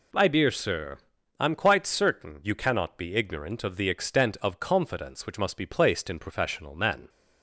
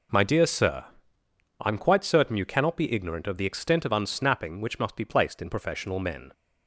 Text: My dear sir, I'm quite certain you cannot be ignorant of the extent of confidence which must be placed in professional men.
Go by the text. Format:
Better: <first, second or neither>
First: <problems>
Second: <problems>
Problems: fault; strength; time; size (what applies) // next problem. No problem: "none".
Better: first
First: none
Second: says "unsnapping" for "confidence"; at 3.9 s